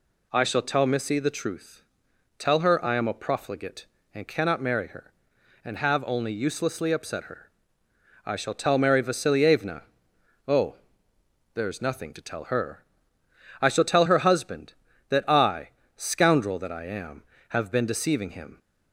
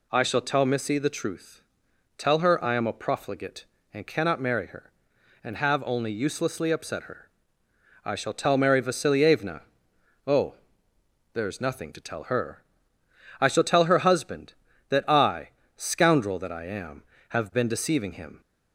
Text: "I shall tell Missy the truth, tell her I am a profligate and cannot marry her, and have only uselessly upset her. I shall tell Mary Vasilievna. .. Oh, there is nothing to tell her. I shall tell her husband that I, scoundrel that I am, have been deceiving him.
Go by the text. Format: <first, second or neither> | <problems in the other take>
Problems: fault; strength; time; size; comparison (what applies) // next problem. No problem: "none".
neither | none